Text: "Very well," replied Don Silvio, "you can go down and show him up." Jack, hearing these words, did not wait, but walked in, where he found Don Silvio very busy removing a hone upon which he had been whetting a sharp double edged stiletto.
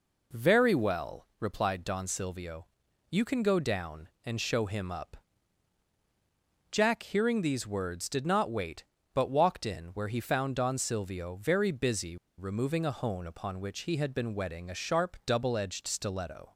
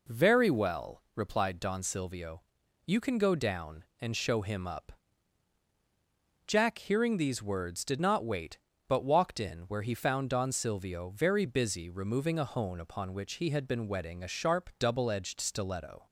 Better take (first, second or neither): second